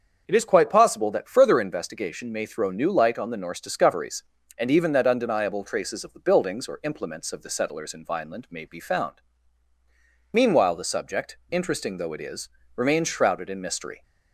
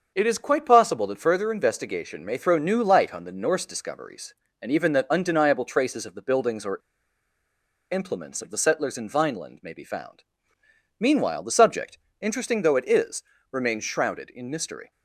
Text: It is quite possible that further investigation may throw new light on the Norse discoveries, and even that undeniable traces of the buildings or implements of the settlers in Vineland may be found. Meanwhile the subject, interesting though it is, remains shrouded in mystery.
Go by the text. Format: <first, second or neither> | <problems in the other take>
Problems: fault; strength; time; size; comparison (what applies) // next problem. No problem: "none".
first | starts louder than the rest; until 1.1 s; 6.5 dB; also in the first // pauses between "or" and "implements"; at 6.7 s; 1.1 s long